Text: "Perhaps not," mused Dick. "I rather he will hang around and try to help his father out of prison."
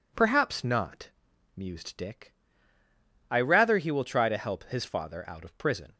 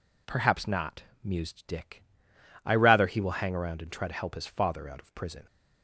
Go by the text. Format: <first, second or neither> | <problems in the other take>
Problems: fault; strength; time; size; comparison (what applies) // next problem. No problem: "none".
second | skips "hang around and"; at 4.0 s